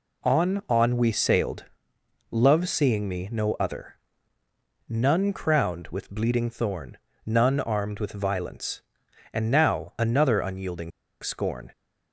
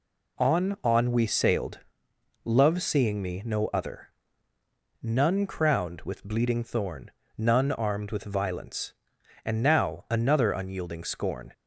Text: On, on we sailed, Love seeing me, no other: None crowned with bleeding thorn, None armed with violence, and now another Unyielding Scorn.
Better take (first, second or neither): second